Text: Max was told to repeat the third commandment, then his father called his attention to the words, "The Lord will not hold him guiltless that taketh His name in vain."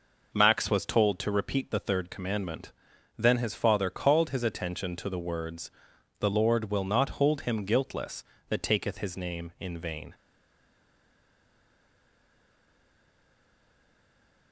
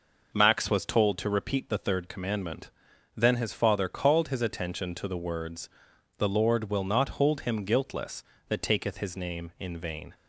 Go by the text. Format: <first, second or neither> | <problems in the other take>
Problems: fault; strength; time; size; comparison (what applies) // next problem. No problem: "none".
second | stays silent after the last word; strong; from 10.1 s on; 4.4 s long